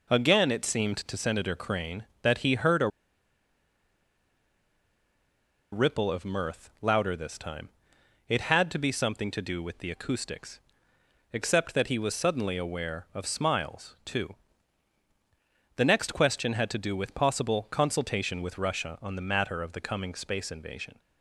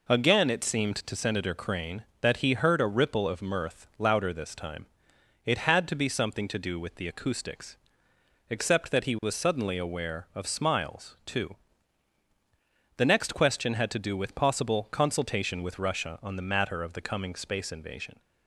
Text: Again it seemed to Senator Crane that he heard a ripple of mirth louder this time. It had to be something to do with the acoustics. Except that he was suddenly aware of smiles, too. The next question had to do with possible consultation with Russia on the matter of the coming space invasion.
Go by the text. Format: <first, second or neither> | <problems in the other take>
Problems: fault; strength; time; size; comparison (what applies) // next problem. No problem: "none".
second | pauses between "a" and "ripple"; strong; at 2.8 s; 2.8 s long